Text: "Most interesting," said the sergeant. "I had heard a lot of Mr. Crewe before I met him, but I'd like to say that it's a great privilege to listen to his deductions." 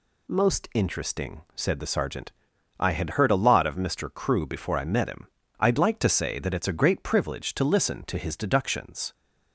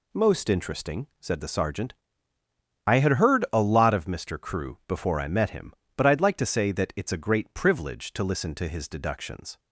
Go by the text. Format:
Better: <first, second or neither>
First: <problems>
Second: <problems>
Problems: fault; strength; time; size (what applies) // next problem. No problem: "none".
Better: second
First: skips "but"; at 5.4 s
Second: none